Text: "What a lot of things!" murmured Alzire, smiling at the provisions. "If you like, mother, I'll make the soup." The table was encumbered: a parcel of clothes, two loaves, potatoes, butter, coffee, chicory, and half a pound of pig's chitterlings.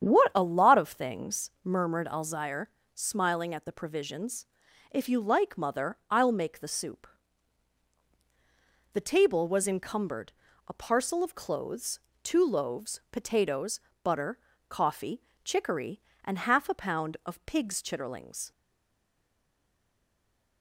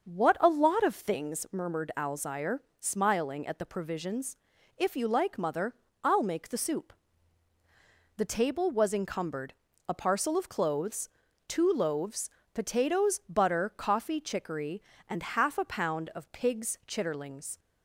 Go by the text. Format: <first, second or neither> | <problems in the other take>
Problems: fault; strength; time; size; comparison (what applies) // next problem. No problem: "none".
second | starts louder than the rest; strong; until 1.0 s; 8.5 dB; also in the second // stays silent after the last word; from 18.5 s on; 2.1 s long